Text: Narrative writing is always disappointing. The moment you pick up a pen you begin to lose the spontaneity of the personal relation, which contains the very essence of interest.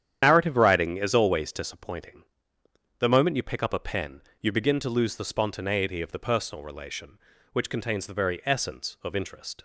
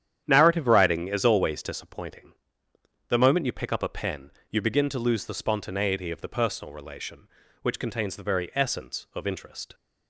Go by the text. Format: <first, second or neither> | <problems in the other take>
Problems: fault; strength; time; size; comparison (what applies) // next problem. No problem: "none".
second | loses the start of "Narrative"; at 0.2 s; 75 ms // starts louder than the rest; strong; until 1.2 s; 10 dB; strong in the second // pauses between "pen" and "you"; slight; at 4.2 s; 0.20 s long; slight in the second